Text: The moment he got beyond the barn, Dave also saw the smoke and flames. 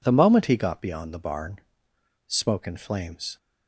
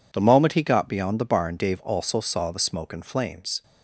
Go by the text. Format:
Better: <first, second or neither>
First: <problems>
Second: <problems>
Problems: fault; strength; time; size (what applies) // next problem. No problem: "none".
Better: second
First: skips "Dave also saw the"; at 1.9 s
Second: none